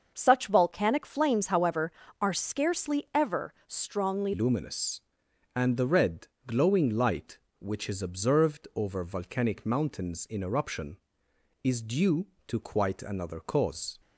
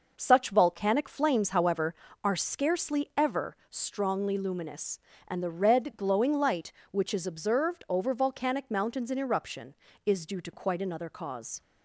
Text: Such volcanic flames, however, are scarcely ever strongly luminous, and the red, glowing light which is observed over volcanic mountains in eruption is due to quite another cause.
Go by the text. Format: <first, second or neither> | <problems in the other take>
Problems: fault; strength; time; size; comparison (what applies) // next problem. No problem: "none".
second | starts louder than the rest; until 1.1 s; 6.5 dB // changes voice at "luminous"; from 4.3 s on; 9.6 s long